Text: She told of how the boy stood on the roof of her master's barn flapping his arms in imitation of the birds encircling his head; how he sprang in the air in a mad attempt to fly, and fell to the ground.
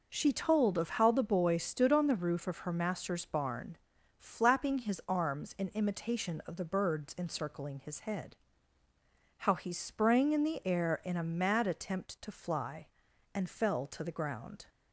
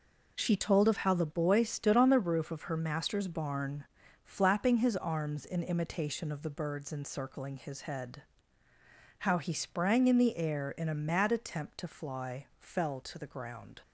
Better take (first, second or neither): first